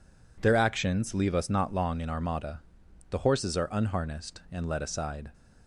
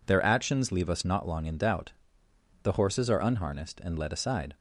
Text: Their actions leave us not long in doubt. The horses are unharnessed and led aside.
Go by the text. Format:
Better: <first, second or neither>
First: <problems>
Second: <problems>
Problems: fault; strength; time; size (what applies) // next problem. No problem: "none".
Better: second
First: says "armada" for "doubt"; at 2.0 s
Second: none